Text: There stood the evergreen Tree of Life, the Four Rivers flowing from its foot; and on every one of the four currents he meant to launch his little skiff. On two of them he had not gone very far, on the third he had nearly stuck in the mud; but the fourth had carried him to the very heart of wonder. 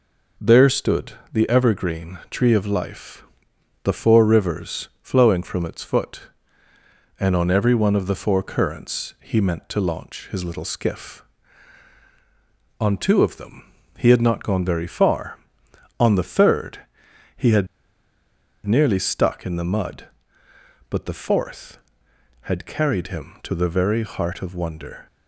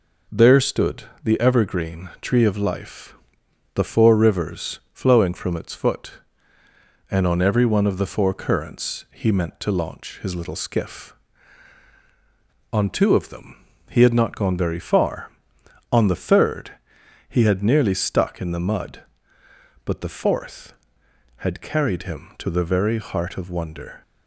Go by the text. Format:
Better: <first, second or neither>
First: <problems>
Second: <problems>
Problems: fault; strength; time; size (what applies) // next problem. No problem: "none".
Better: second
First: pauses between "stood" and "the"; slight; at 1.1 s; 0.18 s long // pauses between "them" and "he"; slight; at 13.7 s; 0.26 s long // pauses between "third" and "he"; noticeable; at 16.8 s; 0.56 s long // pauses between "had" and "nearly"; at 17.6 s; 0.99 s long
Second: pauses between "stood" and "the"; slight; at 1.0 s; 0.18 s long // pauses between "them" and "he"; slight; at 13.6 s; 0.26 s long // pauses between "third" and "he"; noticeable; at 16.7 s; 0.56 s long